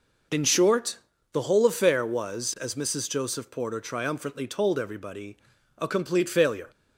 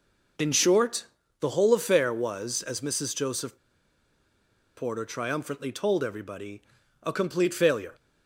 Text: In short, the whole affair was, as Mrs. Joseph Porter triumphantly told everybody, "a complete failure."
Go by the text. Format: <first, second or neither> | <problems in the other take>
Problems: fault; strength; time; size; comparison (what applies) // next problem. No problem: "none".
first | pauses between "Joseph" and "Porter"; at 3.5 s; 1.2 s long